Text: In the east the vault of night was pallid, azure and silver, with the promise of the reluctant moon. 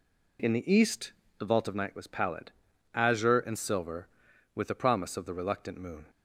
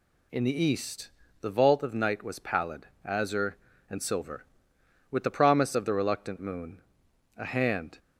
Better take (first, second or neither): first